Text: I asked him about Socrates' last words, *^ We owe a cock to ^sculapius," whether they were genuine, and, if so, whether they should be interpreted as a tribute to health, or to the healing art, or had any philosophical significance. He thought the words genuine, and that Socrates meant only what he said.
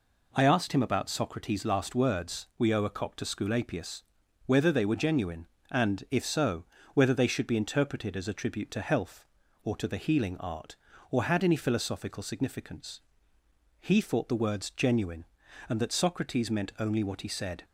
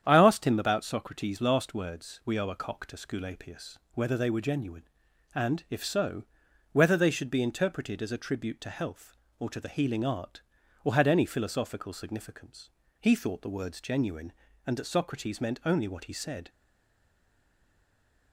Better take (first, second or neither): first